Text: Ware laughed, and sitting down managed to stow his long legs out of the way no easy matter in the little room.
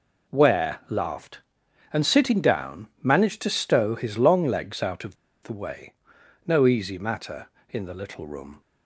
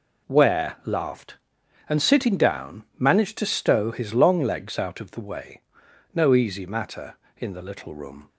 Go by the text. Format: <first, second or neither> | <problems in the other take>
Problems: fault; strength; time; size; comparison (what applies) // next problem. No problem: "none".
second | pauses between "of" and "the"; slight; at 5.1 s; 0.27 s long // pauses between "way" and "no"; noticeable; at 5.9 s; 0.54 s long; noticeable in the second